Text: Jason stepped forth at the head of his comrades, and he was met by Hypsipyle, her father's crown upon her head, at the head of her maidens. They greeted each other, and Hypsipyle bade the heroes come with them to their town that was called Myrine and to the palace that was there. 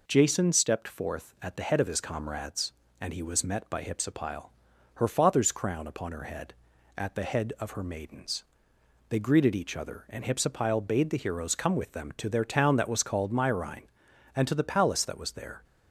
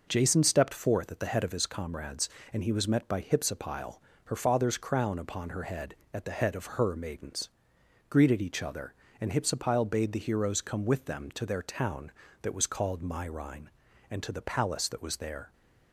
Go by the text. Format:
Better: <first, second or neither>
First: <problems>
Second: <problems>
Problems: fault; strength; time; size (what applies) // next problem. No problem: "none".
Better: first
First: none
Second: skips "They"; at 7.7 s